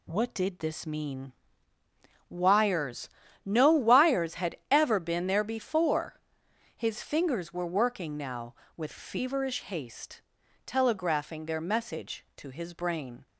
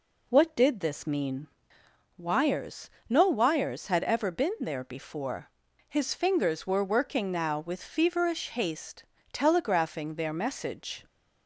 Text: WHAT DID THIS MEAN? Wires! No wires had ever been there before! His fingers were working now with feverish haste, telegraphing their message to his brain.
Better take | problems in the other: first | stops before "to his brain"; at 11.0 s

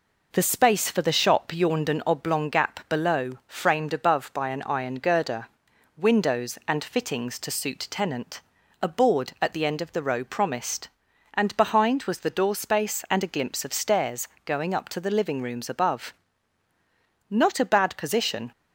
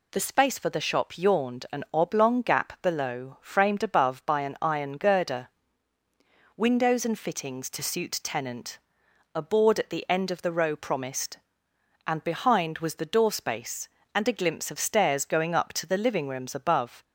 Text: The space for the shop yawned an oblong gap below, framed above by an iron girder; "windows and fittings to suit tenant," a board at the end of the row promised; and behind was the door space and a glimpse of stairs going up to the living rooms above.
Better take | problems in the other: second | pauses between "stairs" and "going"; slight; at 14.2 s; 0.18 s long // goes on to say "Not a bad position"; noticeable; from 17.2 s on; 1.2 s long

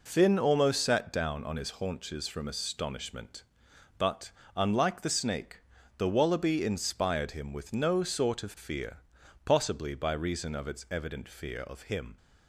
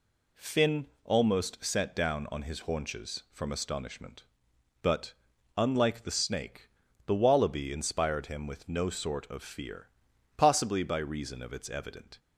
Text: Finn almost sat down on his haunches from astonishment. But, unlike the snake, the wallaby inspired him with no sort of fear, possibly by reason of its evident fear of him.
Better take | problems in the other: first | pauses between "Finn" and "almost"; slight; at 0.8 s; 0.18 s long // stops before "fear of him"; at 12.1 s

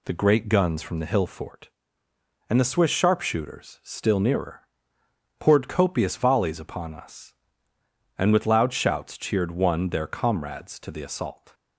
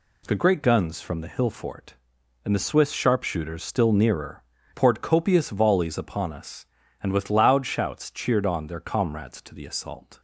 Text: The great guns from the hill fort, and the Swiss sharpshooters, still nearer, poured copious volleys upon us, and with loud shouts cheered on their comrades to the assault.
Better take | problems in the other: second | says "one" for "on"; at 9.5 s

